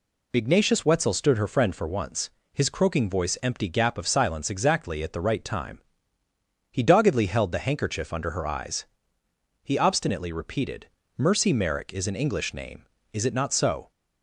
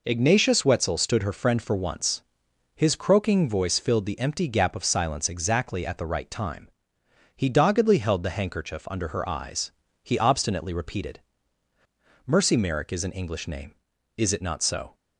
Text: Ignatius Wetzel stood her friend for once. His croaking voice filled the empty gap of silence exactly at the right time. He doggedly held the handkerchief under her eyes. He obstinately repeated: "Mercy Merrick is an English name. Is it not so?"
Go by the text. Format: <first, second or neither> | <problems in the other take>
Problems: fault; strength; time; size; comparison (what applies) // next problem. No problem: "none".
second | skips "filled the"; at 3.3 s